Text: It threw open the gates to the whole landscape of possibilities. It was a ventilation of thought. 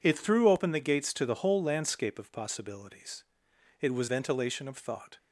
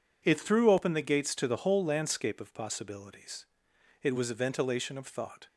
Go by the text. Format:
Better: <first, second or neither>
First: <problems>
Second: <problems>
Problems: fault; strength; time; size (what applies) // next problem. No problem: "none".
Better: second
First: skips "a"; at 4.0 s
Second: none